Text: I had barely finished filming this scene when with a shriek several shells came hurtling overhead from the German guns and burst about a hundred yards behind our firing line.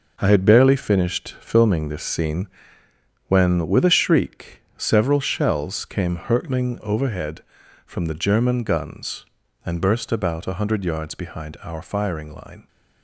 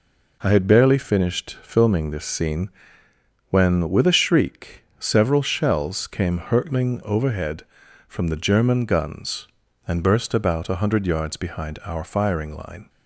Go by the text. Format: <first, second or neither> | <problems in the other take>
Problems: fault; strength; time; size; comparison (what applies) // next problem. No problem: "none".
second | gets quieter; strong; throughout; 8.5 dB // pauses between "scene" and "when"; noticeable; at 2.4 s; 0.80 s long; noticeable in the second // pauses between "shriek" and "several"; slight; at 4.6 s; 0.16 s long; slight in the second